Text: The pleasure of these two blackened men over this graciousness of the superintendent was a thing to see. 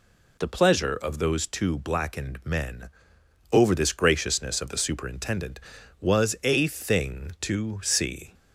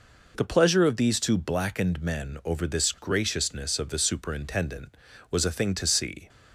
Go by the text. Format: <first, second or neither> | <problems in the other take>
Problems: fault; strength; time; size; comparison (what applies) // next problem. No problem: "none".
second | says "those" for "these"; at 1.1 s // pauses between "men" and "over"; noticeable; at 2.8 s; 0.62 s long